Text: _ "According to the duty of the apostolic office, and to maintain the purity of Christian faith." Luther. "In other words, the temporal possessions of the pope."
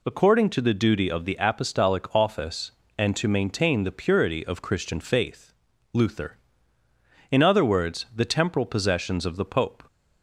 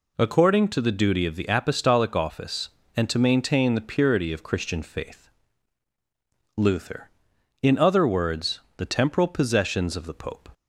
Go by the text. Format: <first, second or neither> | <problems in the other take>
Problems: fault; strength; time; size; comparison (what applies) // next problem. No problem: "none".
neither | none